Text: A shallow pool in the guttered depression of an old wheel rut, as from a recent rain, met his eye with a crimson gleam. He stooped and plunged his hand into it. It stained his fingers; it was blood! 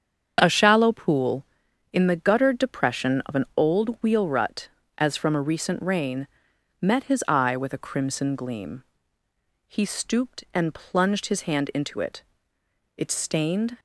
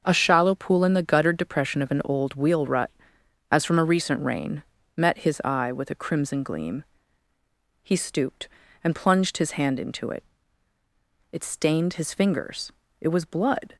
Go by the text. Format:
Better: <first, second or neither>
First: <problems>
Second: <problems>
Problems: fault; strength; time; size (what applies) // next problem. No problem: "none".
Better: second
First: starts louder than the rest; strong; until 1.4 s; 7.5 dB // stops before "his fingers it was blood"; at 13.7 s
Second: starts louder than the rest; until 1.0 s; 6.5 dB